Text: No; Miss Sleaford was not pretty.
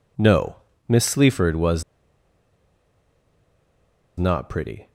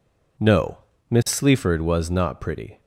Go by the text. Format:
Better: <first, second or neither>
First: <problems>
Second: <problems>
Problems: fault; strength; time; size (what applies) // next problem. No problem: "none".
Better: second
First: pauses between "was" and "not"; strong; at 1.8 s; 2.3 s long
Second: none